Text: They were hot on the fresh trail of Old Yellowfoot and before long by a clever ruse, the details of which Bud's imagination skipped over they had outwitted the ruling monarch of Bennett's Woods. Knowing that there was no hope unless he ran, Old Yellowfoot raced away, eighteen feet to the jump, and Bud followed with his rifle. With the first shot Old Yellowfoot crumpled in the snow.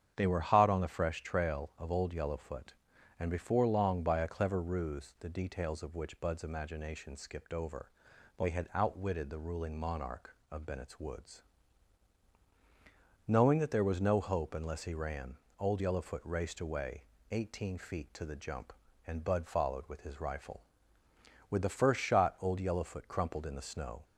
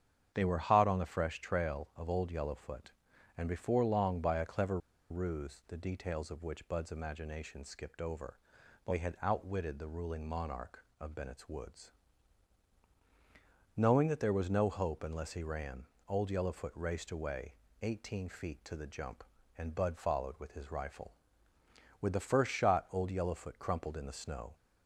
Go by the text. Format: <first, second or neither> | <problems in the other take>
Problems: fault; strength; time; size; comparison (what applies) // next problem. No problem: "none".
first | starts louder than the rest; strong; until 1.3 s; 8.5 dB; strong in the first // pauses between "clever" and "ruse"; slight; at 4.7 s; 0.32 s long // pauses between "over" and "they"; noticeable; at 8.3 s; 0.48 s long; noticeable in the first